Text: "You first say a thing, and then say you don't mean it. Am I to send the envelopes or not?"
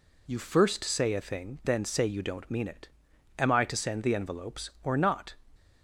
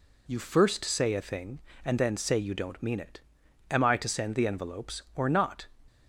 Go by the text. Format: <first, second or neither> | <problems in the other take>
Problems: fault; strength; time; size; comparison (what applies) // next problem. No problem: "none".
second | skips "and"; at 1.6 s